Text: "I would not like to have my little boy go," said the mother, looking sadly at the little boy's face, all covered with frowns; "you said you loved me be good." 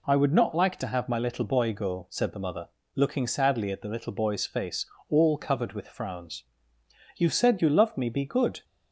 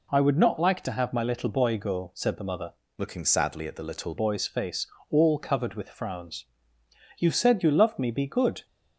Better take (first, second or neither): first